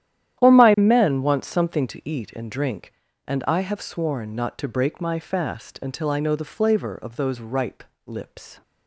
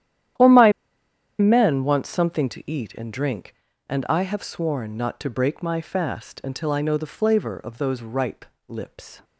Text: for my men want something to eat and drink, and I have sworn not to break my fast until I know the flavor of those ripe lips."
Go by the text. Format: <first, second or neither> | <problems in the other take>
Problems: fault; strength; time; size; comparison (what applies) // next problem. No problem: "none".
first | starts louder than the rest; strong; until 2.0 s; 11 dB; strong in the first // pauses between "my" and "men"; noticeable; at 0.7 s; 0.68 s long // pauses between "ripe" and "lips"; slight; at 8.4 s; 0.24 s long; slight in the first